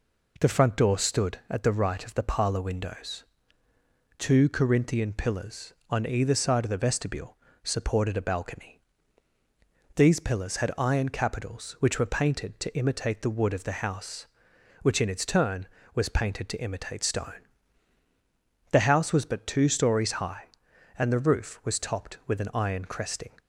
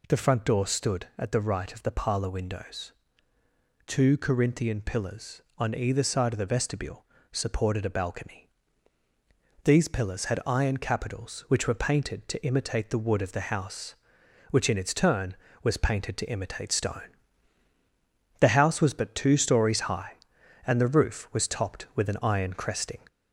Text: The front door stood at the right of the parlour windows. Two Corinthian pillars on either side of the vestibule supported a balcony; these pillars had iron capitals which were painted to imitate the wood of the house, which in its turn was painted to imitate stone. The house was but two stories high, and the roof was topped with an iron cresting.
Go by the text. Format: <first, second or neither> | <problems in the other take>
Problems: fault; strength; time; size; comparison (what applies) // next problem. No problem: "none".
first | gets louder; throughout; 3.5 dB // pauses between "vestibule" and "supported"; slight; at 7.0 s; 0.26 s long; slight in the first